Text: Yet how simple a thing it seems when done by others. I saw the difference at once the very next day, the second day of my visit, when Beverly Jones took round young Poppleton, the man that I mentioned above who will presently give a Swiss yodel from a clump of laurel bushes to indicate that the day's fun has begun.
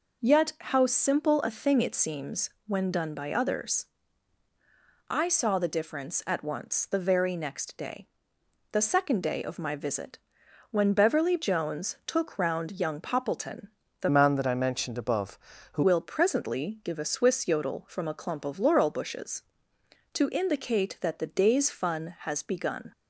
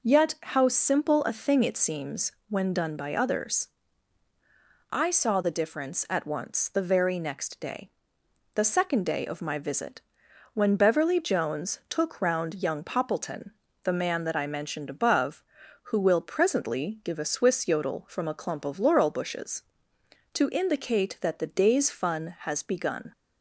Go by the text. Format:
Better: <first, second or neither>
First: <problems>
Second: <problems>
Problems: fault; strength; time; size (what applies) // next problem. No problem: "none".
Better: second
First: pauses between "seems" and "when"; slight; at 2.4 s; 0.18 s long // changes voice from "man" to "who"; from 14.0 to 15.8 s; 1.8 s long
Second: pauses between "seems" and "when"; slight; at 2.3 s; 0.18 s long